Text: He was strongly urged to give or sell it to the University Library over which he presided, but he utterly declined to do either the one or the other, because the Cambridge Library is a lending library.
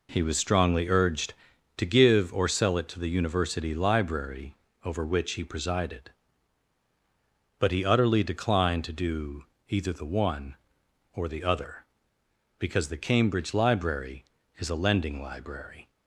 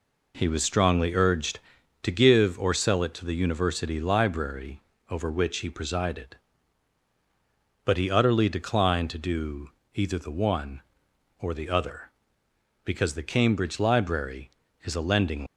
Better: first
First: pauses between "Library" and "over"; slight; at 4.5 s; 0.28 s long // pauses between "do" and "either"; slight; at 9.4 s; 0.24 s long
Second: pauses between "Library" and "over"; slight; at 4.8 s; 0.28 s long // pauses between "do" and "either"; slight; at 9.6 s; 0.24 s long // stops before "library"; at 15.4 s

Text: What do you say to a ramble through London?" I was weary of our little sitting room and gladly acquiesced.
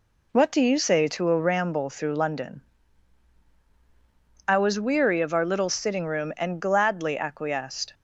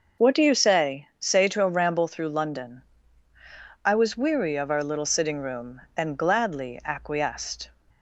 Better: first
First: none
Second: starts louder than the rest; noticeable; until 1.3 s; 6 dB // says "say" twice; at 1.1 s

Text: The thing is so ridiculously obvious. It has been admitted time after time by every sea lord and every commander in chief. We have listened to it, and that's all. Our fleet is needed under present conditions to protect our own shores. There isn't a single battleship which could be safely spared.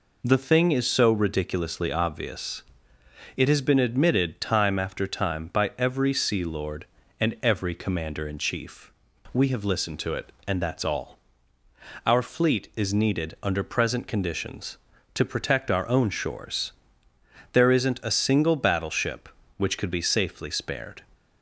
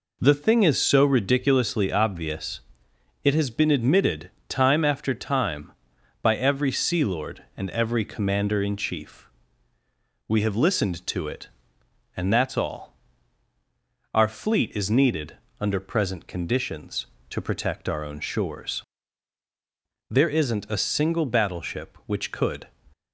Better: first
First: none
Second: pauses between "admitted" and "time"; slight; at 4.3 s; 0.16 s long // pauses between "needed" and "under"; slight; at 15.3 s; 0.24 s long // stops before "be safely spared"; at 22.9 s

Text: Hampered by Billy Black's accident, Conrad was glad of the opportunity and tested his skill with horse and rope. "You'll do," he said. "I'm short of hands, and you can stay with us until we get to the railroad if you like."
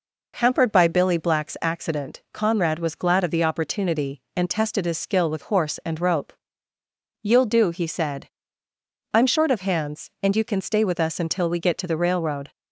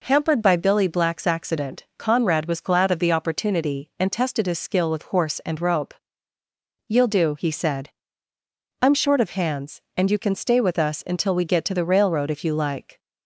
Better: second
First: stops before "if you like"; at 12.5 s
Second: none

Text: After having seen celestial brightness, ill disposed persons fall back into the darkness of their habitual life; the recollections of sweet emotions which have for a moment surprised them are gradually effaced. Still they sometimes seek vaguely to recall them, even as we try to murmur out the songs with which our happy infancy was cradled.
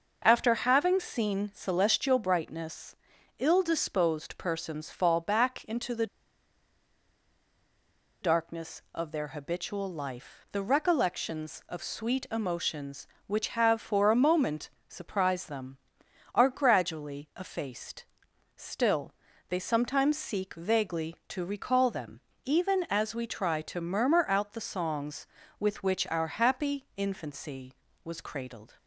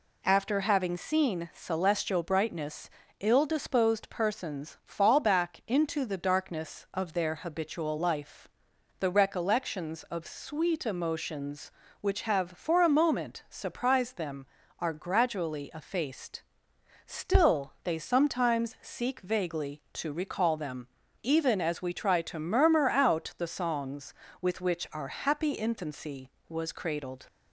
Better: second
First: pauses between "the" and "darkness"; strong; at 6.0 s; 2.1 s long // pauses between "moment" and "surprised"; slight; at 14.6 s; 0.18 s long // pauses between "Still" and "they"; slight; at 19.1 s; 0.34 s long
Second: none

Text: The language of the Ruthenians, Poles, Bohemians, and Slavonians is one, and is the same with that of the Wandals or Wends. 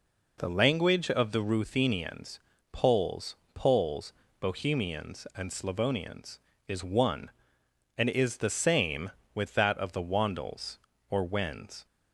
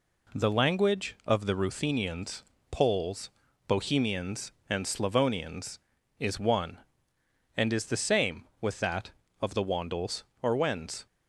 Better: second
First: says "Poles" twice; at 3.5 s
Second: none

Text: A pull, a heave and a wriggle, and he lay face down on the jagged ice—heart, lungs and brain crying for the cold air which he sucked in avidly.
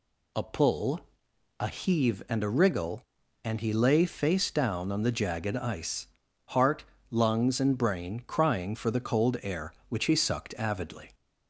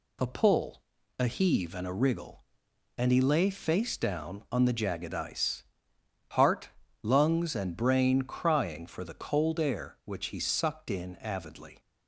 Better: second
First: skips "in"; at 10.5 s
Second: none

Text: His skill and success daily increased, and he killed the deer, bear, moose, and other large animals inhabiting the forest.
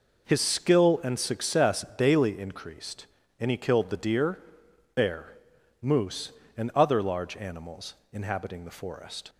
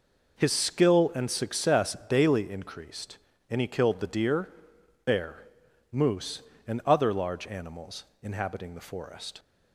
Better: neither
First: pauses between "animals" and "inhabiting"; slight; at 7.9 s; 0.18 s long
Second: pauses between "animals" and "inhabiting"; slight; at 8.0 s; 0.18 s long

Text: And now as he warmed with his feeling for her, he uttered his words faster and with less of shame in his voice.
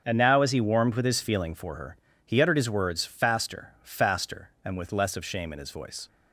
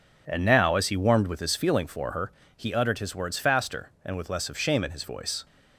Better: second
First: starts louder than the rest; strong; until 1.0 s; 7.5 dB // says "faster" twice; at 3.8 s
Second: none

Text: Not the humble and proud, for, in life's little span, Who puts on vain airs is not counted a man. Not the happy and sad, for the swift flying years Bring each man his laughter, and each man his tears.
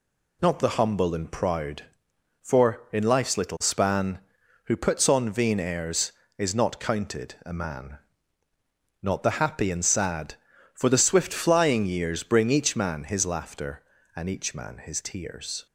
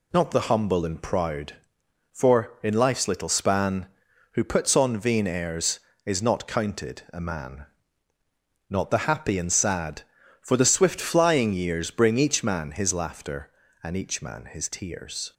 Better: neither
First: none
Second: none

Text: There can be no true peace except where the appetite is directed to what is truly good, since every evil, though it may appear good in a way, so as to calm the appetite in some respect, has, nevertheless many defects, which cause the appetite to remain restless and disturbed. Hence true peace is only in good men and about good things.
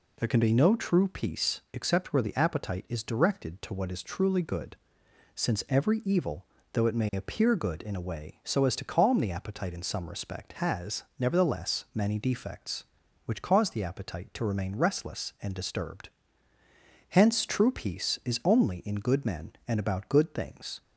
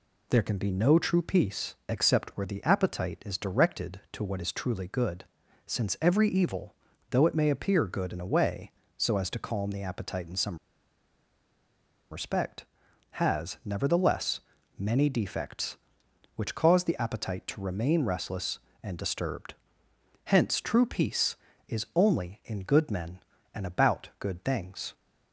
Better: first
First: none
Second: pauses between "some" and "respect"; strong; at 10.5 s; 1.5 s long // pauses between "nevertheless" and "many"; slight; at 14.4 s; 0.36 s long

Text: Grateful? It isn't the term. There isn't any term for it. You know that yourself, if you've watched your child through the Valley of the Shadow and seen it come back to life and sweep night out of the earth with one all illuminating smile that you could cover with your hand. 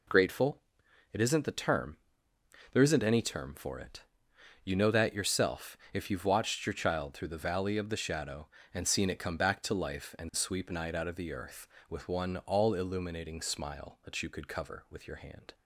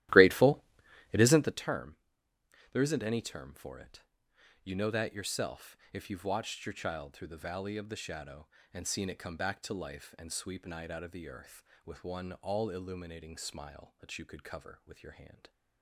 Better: first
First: none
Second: starts louder than the rest; strong; until 1.7 s; 14.5 dB

